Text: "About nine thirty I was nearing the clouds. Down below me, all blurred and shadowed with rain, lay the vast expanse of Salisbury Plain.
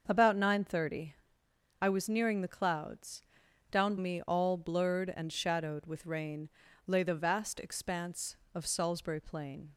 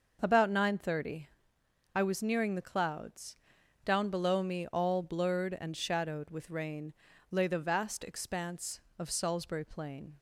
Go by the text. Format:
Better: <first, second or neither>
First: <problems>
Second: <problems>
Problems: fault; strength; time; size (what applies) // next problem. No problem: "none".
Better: second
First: starts louder than the rest; until 1.0 s; 6.5 dB // pauses between "thirty" and "I"; noticeable; at 1.1 s; 0.66 s long // skips "below"; at 3.9 s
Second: starts louder than the rest; until 1.2 s; 6.5 dB // pauses between "thirty" and "I"; noticeable; at 1.2 s; 0.66 s long